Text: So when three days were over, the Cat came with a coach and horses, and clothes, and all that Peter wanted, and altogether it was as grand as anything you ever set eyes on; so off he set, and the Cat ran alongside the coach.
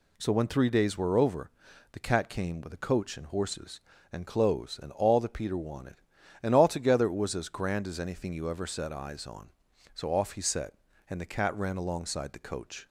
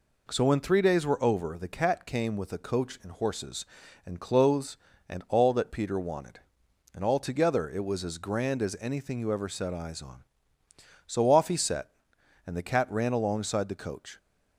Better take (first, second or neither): neither